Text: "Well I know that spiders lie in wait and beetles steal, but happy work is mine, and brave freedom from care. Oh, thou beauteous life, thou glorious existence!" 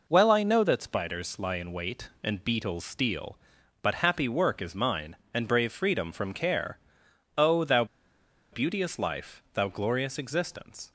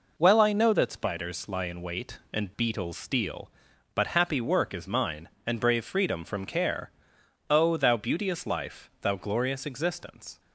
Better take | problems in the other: second | pauses between "thou" and "beauteous"; noticeable; at 7.8 s; 0.67 s long

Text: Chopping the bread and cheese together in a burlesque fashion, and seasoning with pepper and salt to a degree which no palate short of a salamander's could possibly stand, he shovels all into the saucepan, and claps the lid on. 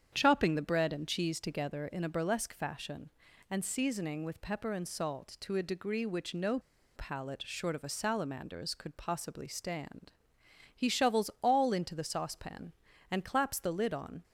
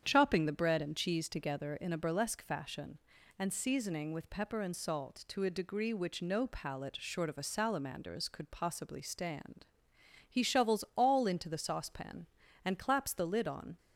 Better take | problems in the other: second | starts louder than the rest; strong; until 1.1 s; 8.5 dB; strong in the second // pauses between "no" and "palate"; at 6.5 s; 0.36 s long

